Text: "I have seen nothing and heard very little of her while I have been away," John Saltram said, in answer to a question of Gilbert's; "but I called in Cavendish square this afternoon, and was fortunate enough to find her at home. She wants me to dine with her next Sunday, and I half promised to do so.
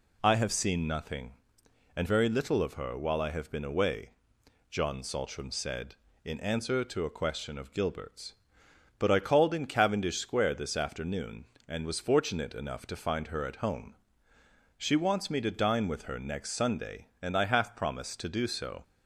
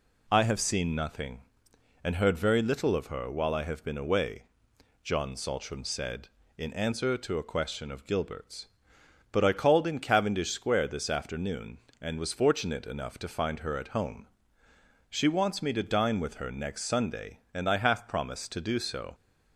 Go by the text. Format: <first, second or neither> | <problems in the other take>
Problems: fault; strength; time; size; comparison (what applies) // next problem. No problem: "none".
second | skips "heard"; at 2.0 s